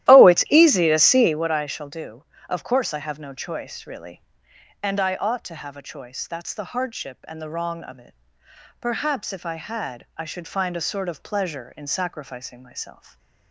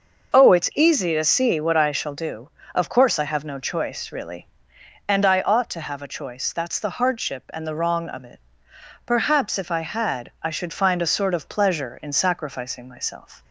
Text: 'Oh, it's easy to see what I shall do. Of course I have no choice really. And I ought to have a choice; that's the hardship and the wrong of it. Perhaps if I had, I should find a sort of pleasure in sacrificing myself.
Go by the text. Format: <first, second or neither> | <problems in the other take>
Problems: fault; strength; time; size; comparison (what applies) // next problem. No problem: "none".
second | starts louder than the rest; strong; until 1.5 s; 13.5 dB